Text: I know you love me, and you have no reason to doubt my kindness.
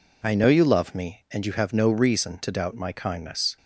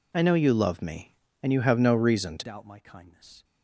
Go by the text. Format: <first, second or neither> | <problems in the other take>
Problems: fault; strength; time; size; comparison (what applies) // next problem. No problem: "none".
first | changes voice at "doubt"; from 2.4 s on; 1.0 s long